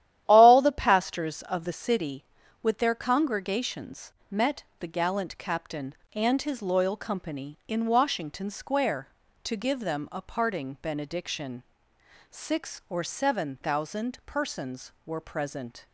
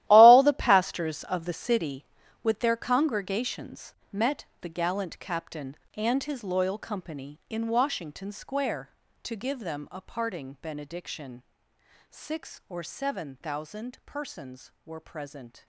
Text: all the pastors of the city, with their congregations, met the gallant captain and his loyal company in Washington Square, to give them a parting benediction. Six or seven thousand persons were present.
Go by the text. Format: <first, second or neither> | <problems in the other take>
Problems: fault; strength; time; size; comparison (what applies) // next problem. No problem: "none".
first | gets quieter; strong; throughout; 14 dB // starts louder than the rest; strong; until 1.0 s; 14.5 dB; strong in the first // pauses between "met" and "the"; slight; at 4.4 s; 0.16 s long; slight in the first